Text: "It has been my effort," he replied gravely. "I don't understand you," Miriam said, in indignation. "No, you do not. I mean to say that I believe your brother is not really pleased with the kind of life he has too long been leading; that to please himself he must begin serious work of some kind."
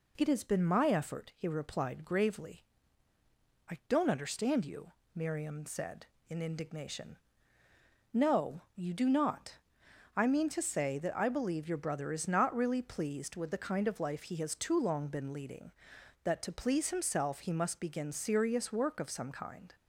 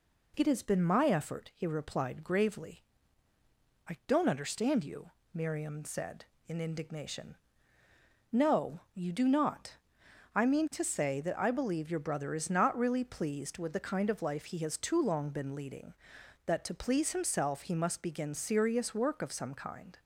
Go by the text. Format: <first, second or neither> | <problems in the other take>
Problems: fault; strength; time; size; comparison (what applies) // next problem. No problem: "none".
neither | none